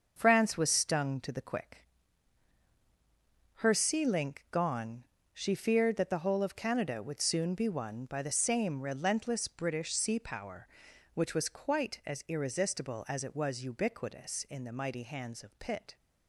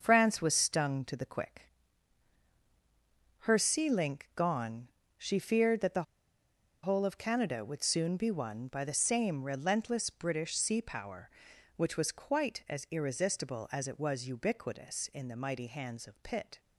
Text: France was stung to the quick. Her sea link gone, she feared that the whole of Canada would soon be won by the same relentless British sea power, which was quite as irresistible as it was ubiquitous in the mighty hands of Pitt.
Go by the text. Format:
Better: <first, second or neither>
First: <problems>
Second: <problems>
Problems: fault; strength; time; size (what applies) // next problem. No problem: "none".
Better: first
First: starts louder than the rest; until 1.1 s; 6.5 dB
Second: starts louder than the rest; until 1.0 s; 6.5 dB // pauses between "the" and "whole"; noticeable; at 6.0 s; 0.81 s long